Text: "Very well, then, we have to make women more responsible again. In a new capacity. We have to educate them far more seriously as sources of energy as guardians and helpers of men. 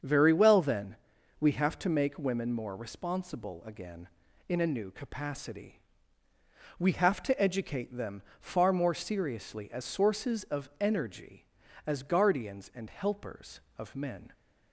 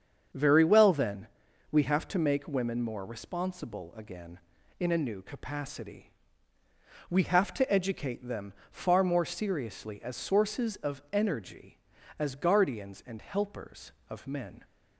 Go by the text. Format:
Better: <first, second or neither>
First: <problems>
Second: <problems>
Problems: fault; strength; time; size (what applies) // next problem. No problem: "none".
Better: neither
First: starts louder than the rest; until 1.4 s; 7 dB // pauses between "them" and "far"; slight; at 8.2 s; 0.18 s long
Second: starts louder than the rest; until 1.7 s; 7 dB // pauses between "them" and "far"; slight; at 8.5 s; 0.18 s long